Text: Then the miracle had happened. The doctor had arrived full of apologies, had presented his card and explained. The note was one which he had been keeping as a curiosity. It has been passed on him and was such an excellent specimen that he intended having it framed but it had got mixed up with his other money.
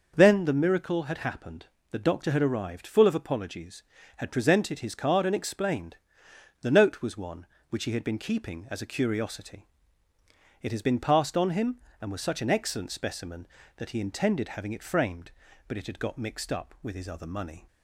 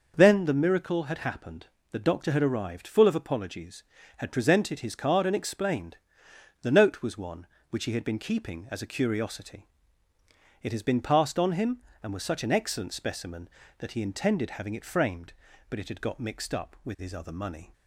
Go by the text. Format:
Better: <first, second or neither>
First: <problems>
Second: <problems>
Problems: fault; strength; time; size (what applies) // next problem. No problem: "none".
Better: neither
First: none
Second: none